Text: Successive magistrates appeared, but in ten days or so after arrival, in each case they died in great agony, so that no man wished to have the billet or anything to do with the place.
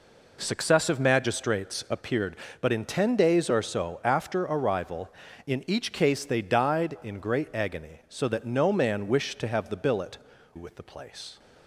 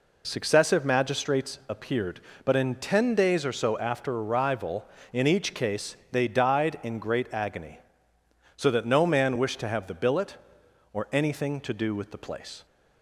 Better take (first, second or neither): second